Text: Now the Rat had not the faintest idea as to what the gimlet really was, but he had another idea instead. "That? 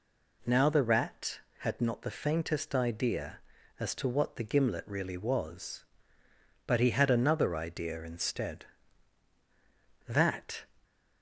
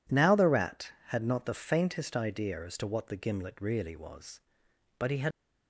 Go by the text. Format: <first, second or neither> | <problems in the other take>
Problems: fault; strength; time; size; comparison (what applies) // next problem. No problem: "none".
first | stops before "another idea instead That"; at 5.3 s